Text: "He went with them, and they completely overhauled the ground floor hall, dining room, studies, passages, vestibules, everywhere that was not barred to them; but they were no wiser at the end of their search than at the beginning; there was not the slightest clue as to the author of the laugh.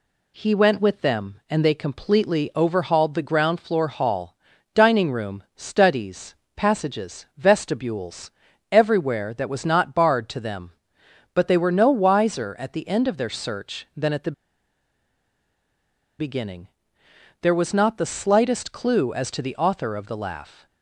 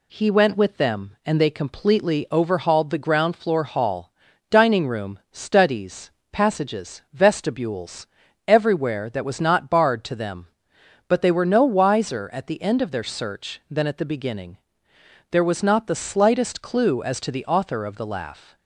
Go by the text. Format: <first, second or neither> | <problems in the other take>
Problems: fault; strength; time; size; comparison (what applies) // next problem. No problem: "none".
second | pauses between "the" and "beginning"; strong; at 14.3 s; 1.8 s long